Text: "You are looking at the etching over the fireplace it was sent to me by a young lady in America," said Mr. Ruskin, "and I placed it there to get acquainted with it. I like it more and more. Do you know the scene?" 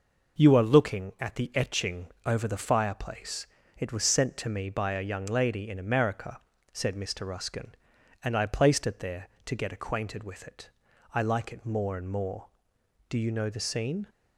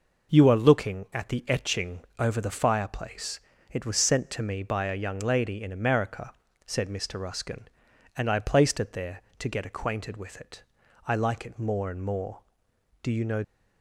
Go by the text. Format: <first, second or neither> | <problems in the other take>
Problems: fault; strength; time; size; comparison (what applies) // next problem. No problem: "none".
first | pauses between "fireplace" and "it"; slight; at 3.4 s; 0.32 s long; slight in the first // stops before "the scene"; at 13.4 s